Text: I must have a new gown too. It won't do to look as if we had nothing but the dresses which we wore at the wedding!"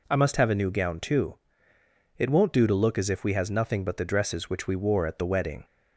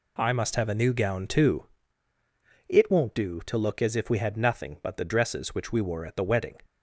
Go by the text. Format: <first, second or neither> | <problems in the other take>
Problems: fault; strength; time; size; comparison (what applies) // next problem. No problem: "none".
second | says "has" for "had"; at 3.3 s